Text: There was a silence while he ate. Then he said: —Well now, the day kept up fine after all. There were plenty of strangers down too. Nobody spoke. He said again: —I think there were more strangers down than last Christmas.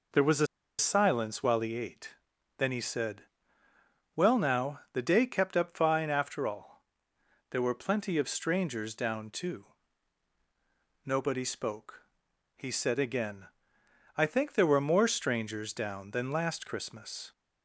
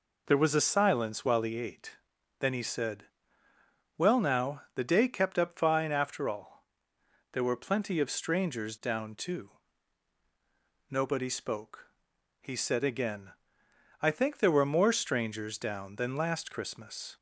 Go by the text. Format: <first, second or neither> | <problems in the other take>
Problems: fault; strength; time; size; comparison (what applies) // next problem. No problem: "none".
second | pauses between "a" and "silence"; slight; at 0.4 s; 0.32 s long